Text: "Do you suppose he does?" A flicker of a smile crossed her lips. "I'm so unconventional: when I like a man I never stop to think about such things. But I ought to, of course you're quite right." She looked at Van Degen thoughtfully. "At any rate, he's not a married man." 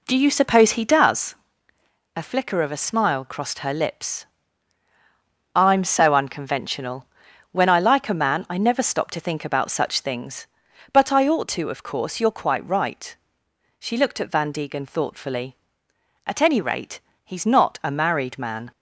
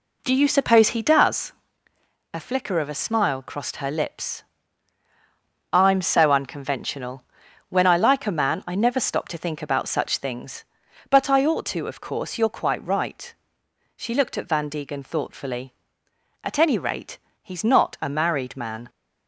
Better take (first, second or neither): neither